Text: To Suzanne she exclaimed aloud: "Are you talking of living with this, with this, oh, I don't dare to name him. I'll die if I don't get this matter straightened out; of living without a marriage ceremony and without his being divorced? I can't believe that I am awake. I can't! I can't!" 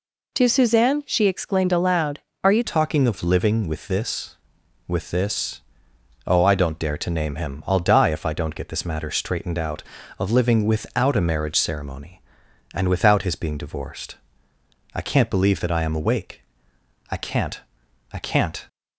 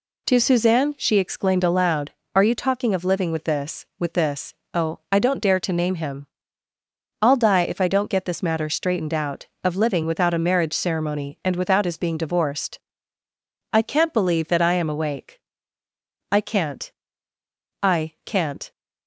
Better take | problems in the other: second | changes voice at "talking"; from 2.6 s on; 16.0 s long

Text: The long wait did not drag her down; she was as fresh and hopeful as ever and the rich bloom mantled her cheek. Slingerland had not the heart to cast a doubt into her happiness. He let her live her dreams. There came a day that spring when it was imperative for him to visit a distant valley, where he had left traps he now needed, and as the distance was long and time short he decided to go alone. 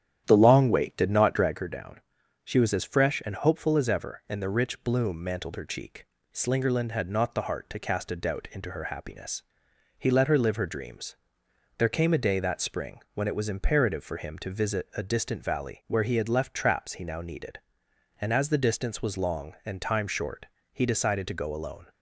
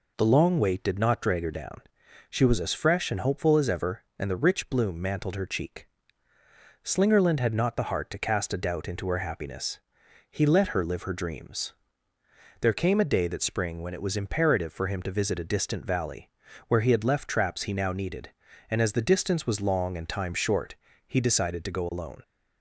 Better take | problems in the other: second | starts louder than the rest; strong; until 1.6 s; 10 dB // pauses between "short" and "he"; slight; at 20.4 s; 0.26 s long; slight in the second

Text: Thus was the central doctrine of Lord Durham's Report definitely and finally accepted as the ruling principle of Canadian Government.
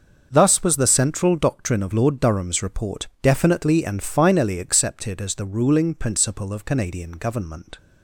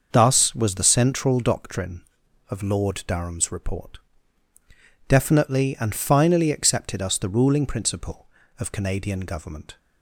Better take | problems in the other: first | starts louder than the rest; until 1.1 s; 6 dB; also in the first // pauses between "Report" and "definitely"; at 3.9 s; 1.1 s long // says "us" for "as"; at 7.0 s

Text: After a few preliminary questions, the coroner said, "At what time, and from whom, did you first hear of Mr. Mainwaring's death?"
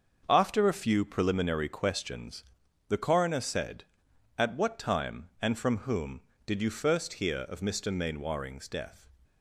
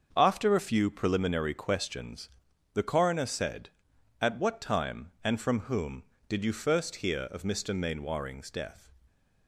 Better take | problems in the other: neither | starts louder than the rest; the same in both

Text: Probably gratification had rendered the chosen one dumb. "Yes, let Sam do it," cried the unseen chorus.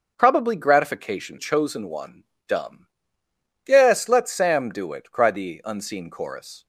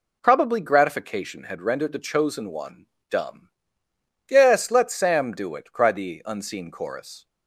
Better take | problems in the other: second | starts louder than the rest; until 1.1 s; 6.5 dB // skips "had rendered the"; at 1.3 s // pauses between "one" and "dumb"; slight; at 2.2 s; 0.22 s long; slight in the second

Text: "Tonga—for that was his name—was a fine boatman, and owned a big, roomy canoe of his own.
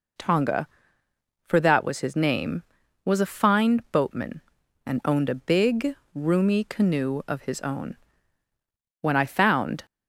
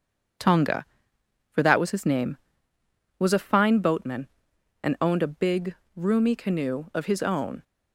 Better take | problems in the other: second | goes on to say "When I found"; noticeable; from 9.0 s on; 0.82 s long

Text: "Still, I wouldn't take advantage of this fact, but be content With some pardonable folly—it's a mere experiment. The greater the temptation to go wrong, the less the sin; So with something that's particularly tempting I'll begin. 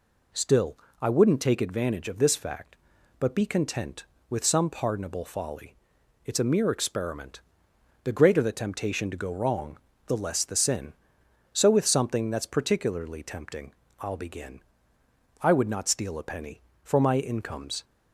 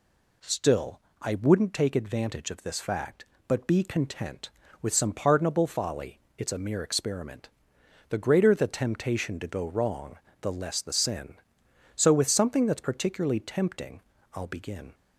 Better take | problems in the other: second | pauses between "tempting" and "I'll"; slight; at 13.7 s; 0.26 s long; slight in the second // goes on to say "I would not steal a penny for my income's"; strong; from 15.4 s on; 2.4 s long

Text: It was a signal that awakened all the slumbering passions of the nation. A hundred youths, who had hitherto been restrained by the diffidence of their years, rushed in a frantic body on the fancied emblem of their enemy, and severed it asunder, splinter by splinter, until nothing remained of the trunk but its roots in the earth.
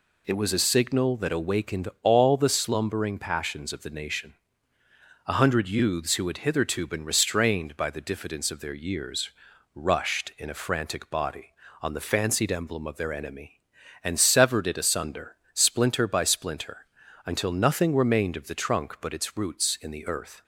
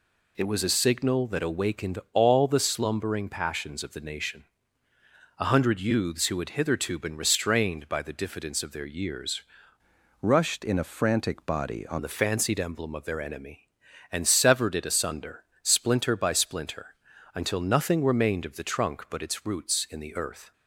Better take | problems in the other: first | changes voice from "rushed" to "on"; from 10.2 to 11.9 s; 1.7 s long

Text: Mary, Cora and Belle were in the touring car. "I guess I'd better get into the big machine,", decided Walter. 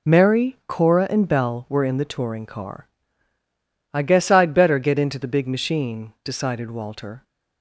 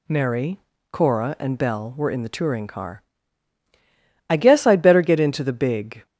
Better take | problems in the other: first | stops before "machine decided Walter"; at 6.0 s

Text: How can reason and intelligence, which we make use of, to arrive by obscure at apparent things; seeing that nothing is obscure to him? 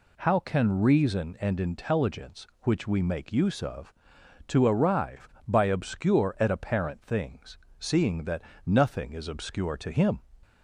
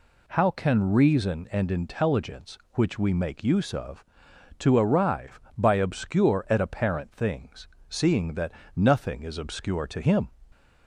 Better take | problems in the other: neither | pauses between "that" and "nothing"; slight; the same in both

